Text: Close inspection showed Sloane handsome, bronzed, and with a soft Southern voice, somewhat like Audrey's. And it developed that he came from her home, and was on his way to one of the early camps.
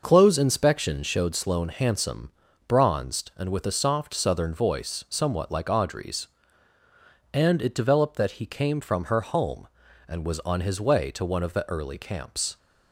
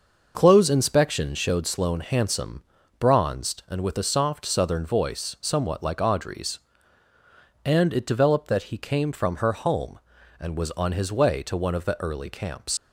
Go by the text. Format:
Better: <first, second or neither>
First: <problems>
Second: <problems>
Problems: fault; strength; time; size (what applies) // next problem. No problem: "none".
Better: first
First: none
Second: leaves "camps" unfinished; at 12.7 s; 130 ms